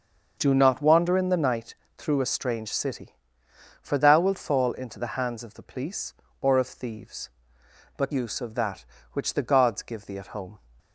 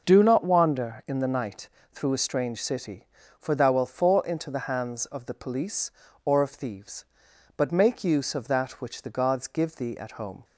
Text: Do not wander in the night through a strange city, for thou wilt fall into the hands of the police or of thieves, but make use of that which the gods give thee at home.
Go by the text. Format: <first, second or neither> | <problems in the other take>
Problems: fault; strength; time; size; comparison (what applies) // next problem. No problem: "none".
second | starts louder than the rest; until 1.3 s; 6.5 dB // pauses between "night" and "through"; slight; at 1.7 s; 0.22 s long; slight in the second // skips "make"; at 8.1 s